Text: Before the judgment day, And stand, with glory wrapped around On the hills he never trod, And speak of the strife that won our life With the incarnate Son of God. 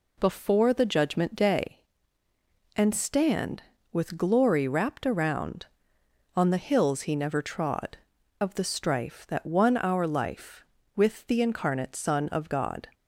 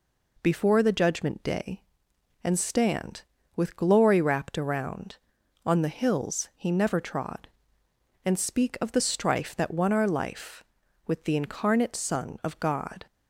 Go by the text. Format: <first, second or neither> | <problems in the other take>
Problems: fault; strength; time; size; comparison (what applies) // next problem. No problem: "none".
second | skips "And speak"; at 8.1 s